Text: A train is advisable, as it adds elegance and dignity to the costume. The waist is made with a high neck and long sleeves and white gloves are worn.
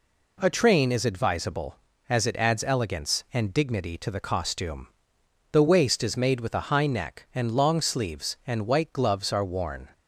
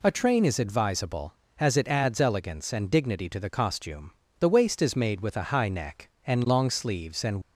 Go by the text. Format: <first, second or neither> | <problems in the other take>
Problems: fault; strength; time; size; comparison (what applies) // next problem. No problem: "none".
first | stops before "white gloves are worn"; at 7.4 s